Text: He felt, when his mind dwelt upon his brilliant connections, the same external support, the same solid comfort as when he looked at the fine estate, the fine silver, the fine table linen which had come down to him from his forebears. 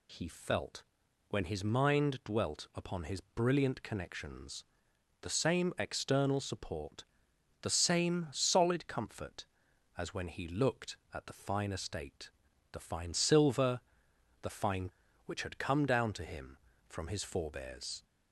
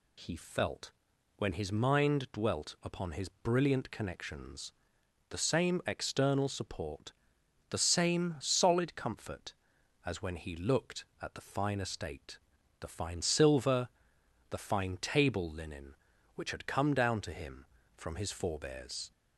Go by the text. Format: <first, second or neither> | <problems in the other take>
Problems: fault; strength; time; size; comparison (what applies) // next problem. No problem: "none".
second | skips "table linen"; at 15.0 s